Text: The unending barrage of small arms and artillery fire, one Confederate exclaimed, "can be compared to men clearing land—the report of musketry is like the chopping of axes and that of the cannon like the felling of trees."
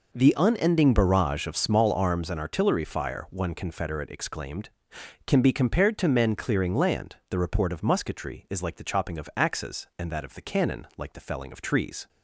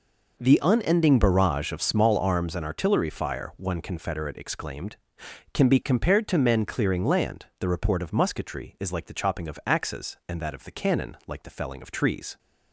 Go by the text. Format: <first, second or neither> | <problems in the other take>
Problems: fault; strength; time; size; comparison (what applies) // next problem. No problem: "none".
neither | none